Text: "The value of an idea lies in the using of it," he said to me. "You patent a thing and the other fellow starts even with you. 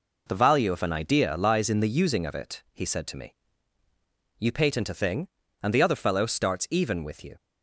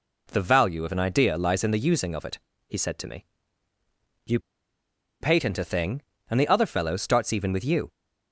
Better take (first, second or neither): first